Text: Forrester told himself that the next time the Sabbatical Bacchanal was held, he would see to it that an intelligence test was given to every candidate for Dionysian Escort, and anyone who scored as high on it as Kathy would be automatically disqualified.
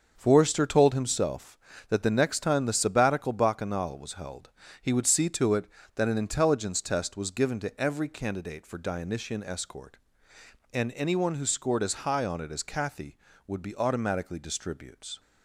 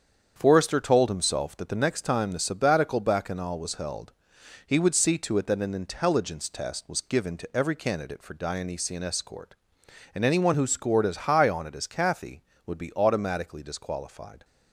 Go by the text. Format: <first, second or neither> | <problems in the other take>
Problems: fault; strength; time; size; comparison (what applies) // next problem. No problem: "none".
second | starts louder than the rest; until 1.1 s; 7 dB; strong in the second // says "distributes" for "disqualified"; at 14.3 s